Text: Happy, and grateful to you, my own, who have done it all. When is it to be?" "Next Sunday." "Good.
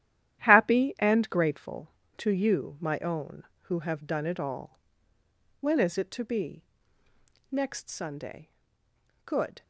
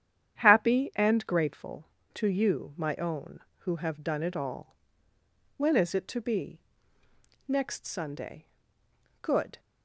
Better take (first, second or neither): second